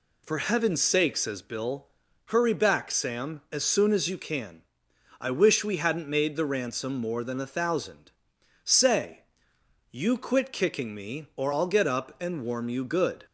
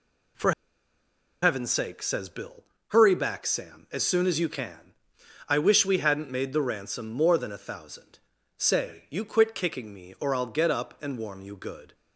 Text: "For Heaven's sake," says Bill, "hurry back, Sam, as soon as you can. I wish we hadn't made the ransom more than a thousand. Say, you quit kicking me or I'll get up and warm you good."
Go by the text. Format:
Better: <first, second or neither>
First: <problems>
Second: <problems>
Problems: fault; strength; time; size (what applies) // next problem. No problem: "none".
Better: first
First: none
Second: pauses between "For" and "Heaven's"; noticeable; at 0.5 s; 0.90 s long